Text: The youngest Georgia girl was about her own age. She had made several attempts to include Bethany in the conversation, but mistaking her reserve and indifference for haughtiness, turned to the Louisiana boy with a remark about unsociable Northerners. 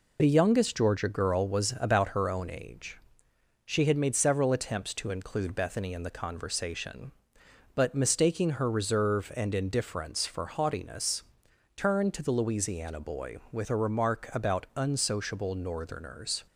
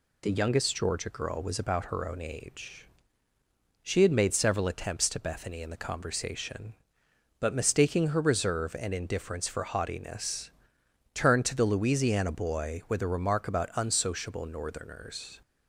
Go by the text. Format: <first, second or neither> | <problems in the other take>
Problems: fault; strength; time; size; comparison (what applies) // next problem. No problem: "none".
first | skips "include"; at 5.1 s